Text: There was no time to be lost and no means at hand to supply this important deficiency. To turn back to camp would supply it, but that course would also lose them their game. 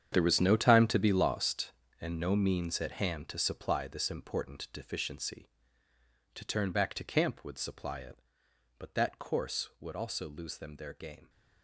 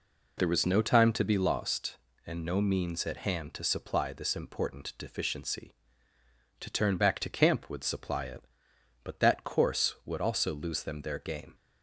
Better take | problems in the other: second | gets quieter; strong; throughout; 14.5 dB

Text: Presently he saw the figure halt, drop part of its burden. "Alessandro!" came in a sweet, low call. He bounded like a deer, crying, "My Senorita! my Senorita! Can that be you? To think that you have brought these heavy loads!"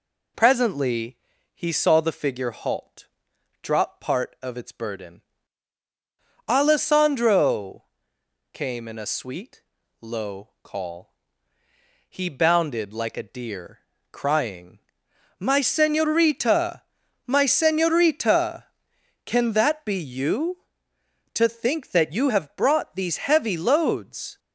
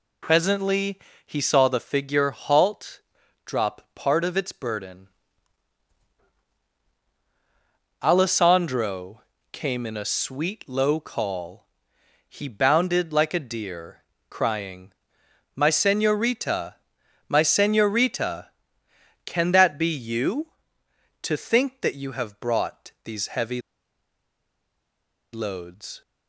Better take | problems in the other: first | pauses between "Presently" and "he"; slight; at 0.9 s; 0.28 s long; also in the first // pauses between "heavy" and "loads"; strong; at 23.5 s; 1.7 s long

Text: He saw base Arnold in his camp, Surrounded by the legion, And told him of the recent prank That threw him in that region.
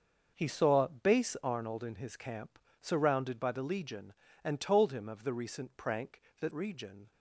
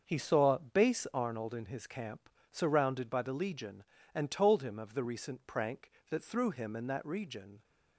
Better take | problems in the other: second | starts louder than the rest; until 1.3 s; 6 dB; also in the second // skips "threw him in that"; at 6.5 s

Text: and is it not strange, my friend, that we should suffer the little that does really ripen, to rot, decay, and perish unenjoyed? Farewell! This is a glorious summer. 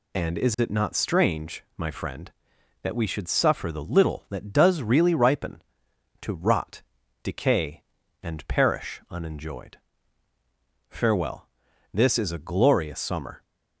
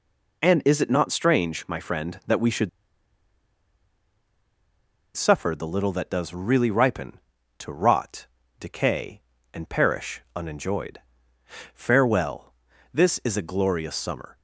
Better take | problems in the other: first | pauses between "should" and "suffer"; strong; at 2.6 s; 2.4 s long

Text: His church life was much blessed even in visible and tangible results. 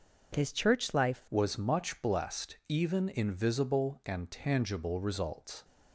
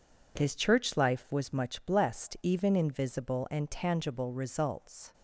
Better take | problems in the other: second | changes voice at "was"; from 1.2 s on; 4.4 s long

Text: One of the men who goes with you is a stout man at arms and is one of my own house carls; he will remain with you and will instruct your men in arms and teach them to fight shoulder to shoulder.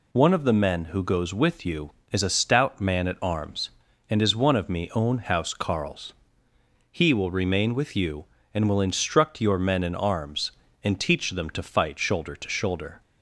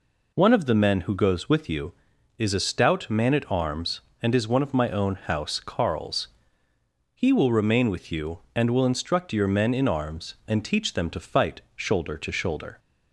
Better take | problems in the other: second | says "me" for "my"; at 4.6 s

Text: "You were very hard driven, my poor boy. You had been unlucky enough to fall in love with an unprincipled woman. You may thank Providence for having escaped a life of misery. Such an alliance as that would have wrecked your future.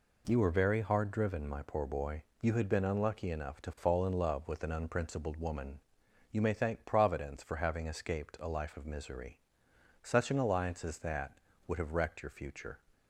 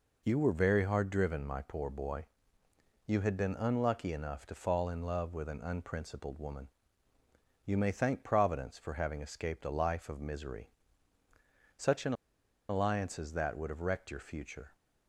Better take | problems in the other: first | pauses between "an" and "alliance"; noticeable; at 12.1 s; 0.55 s long

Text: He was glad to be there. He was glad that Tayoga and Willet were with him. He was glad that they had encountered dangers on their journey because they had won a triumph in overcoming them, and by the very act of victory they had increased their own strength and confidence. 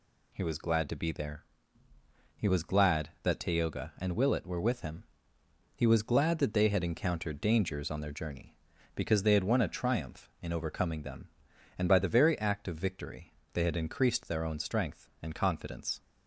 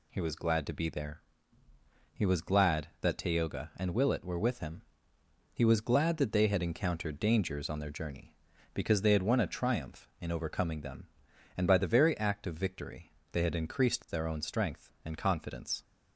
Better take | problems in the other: neither | pauses between "victory" and "they"; slight; the same in both

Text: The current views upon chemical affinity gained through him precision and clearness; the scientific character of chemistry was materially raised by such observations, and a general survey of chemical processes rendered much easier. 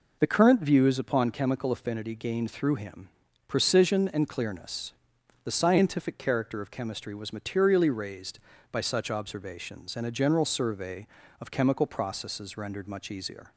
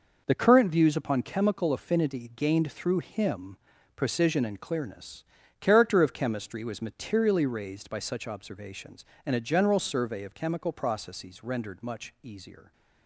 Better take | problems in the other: first | pauses between "him" and "precision"; at 3.5 s; 0.40 s long; also in the first // skips "the scientific"; at 5.4 s

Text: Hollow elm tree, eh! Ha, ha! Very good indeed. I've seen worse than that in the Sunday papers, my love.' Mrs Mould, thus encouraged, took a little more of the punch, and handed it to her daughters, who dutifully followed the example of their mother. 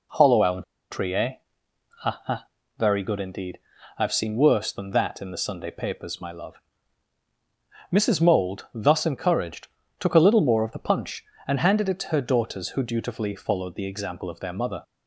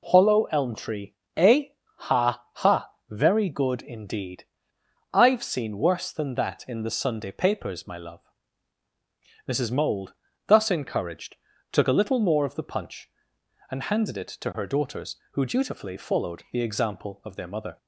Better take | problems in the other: second | pauses between "elm" and "tree"; slight; at 0.6 s; 0.30 s long

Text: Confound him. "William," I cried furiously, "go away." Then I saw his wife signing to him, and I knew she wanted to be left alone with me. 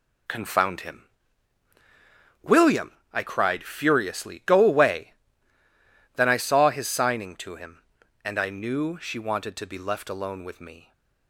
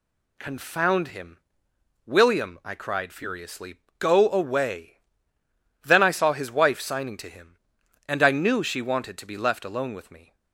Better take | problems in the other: second | skips "wife"; at 6.8 s

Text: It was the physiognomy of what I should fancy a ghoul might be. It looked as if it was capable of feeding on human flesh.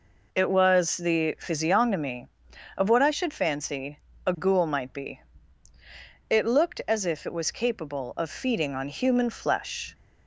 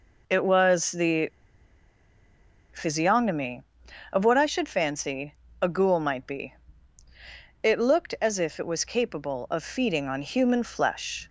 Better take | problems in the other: first | pauses between "the" and "physiognomy"; strong; at 1.2 s; 1.4 s long // pauses between "fancy" and "a"; slight; at 5.3 s; 0.26 s long; slight in the first

